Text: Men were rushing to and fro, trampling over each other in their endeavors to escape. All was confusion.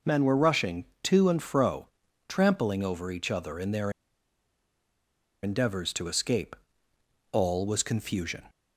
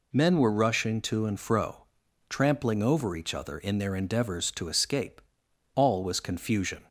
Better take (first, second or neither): second